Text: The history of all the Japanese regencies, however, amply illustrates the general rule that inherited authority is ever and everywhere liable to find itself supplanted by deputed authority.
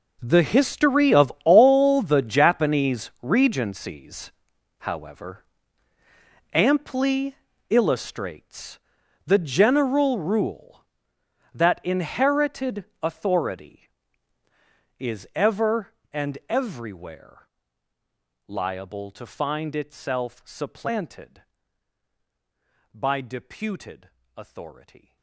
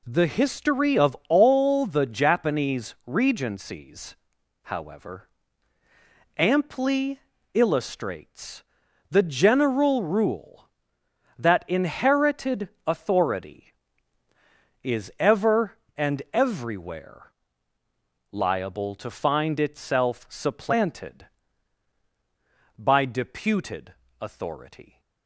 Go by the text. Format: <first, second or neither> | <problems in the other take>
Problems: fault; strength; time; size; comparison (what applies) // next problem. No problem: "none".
second | gets quieter; strong; throughout; 18.5 dB // pauses between "amply" and "illustrates"; slight; at 7.3 s; 0.34 s long; slight in the second // pauses between "illustrates" and "the"; noticeable; at 8.7 s; 0.46 s long; noticeable in the second // pauses between "inherited" and "authority"; slight; at 12.8 s; 0.18 s long; slight in the second // pauses between "everywhere" and "liable"; noticeable; at 17.4 s; 0.98 s long; noticeable in the second // pauses between "deputed" and "authority"; slight; at 24.0 s; 0.26 s long; slight in the second